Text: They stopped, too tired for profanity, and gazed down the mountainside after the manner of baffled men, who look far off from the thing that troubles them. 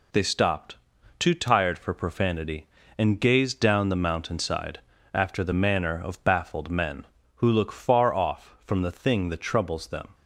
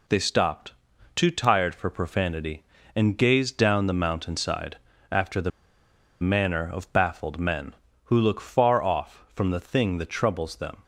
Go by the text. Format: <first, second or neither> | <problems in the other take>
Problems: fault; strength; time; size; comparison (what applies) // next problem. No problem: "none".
first | pauses between "mountainside" and "after"; slight; at 4.7 s; 0.34 s long; slight in the first // pauses between "the" and "manner"; noticeable; at 5.5 s; 0.71 s long